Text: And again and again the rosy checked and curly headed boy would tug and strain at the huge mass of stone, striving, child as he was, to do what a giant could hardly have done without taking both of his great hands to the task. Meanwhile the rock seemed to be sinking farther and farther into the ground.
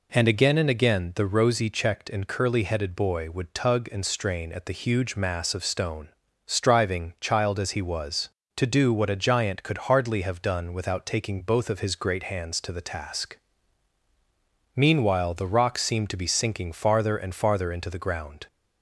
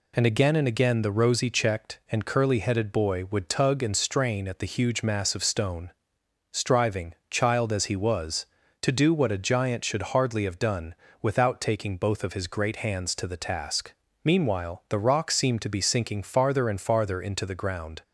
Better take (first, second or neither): first